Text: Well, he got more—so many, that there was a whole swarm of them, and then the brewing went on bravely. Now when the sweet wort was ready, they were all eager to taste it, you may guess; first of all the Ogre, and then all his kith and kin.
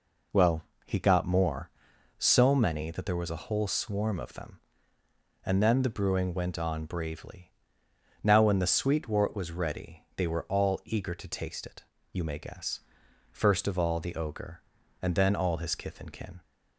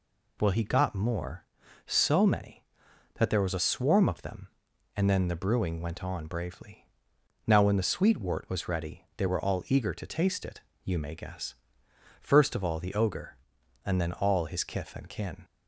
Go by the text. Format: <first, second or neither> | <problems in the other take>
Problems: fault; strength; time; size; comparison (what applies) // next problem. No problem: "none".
first | skips "whole"; at 3.5 s